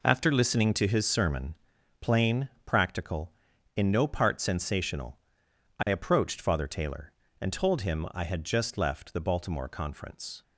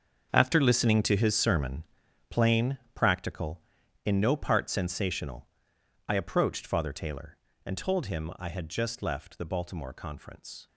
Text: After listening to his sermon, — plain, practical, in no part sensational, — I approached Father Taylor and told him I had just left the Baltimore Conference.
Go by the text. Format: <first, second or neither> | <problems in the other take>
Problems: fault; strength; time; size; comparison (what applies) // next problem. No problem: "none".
first | gets quieter; strong; throughout; 13.5 dB